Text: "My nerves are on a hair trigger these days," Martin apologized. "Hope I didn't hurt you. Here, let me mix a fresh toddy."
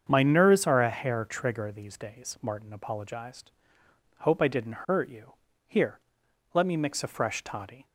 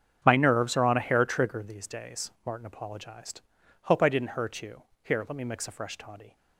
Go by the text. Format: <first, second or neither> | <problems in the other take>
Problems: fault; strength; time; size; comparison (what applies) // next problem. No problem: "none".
second | starts louder than the rest; strong; until 1.1 s; 7.5 dB; strong in the second // skips "on"; at 0.8 s